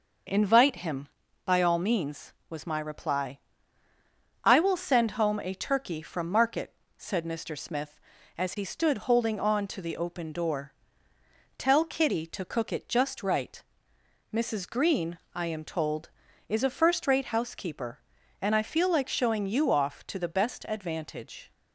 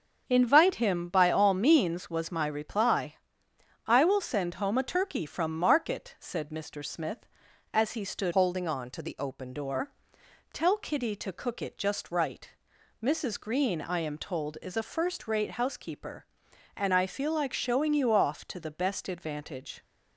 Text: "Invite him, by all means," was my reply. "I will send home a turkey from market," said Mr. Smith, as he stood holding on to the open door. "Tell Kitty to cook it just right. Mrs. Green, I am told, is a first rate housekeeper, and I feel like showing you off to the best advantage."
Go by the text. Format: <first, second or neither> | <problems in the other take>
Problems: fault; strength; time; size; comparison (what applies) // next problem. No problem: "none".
first | starts louder than the rest; until 1.2 s; 7 dB // changes voice from "holding" to "open"; from 8.3 to 9.5 s; 1.2 s long